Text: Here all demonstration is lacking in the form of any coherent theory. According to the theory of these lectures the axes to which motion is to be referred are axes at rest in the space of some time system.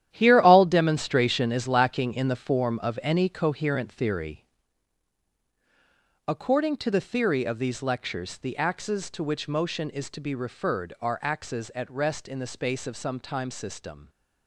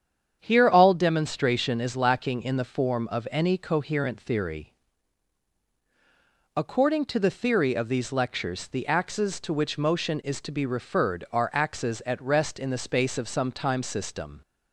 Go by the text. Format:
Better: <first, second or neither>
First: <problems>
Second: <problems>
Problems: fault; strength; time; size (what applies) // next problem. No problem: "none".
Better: second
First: gets quieter; strong; throughout; 11.5 dB // starts louder than the rest; strong; until 1.1 s; 11.5 dB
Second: starts louder than the rest; strong; until 1.4 s; 8 dB